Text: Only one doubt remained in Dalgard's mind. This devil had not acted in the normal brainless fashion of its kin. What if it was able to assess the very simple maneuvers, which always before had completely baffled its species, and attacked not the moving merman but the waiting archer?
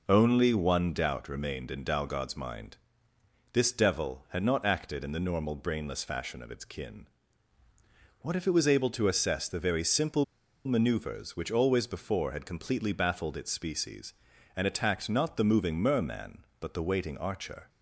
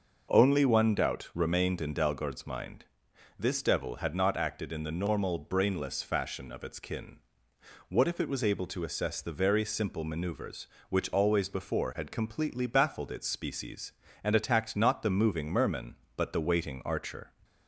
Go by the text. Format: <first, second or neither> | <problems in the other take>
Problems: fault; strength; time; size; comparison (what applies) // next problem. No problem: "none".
second | pauses between "simple" and "maneuvers"; at 10.2 s; 0.41 s long